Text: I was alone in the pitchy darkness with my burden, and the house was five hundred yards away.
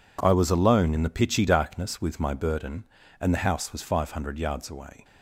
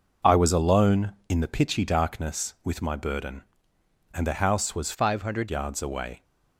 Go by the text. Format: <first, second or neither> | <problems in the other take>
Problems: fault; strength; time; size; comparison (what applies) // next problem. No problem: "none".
first | changes voice from "five" to "hundred"; from 4.9 to 5.4 s; 0.5 s long